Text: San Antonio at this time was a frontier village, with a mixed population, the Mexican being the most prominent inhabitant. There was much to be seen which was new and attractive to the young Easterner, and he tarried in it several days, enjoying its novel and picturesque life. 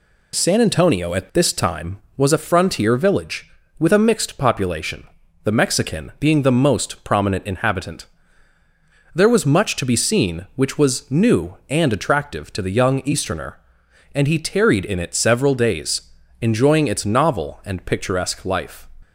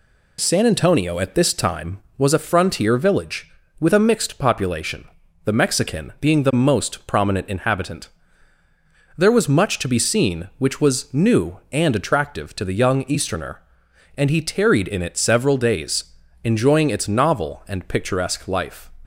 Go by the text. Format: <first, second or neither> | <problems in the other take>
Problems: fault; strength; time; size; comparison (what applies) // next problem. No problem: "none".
neither | none